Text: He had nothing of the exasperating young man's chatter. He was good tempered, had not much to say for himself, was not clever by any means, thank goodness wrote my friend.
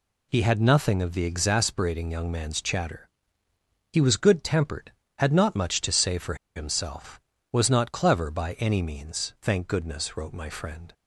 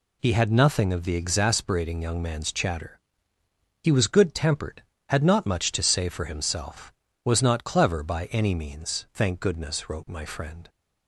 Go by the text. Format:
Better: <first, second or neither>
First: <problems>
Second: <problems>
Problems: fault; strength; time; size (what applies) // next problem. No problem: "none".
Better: second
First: pauses between "for" and "himself"; slight; at 6.3 s; 0.21 s long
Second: none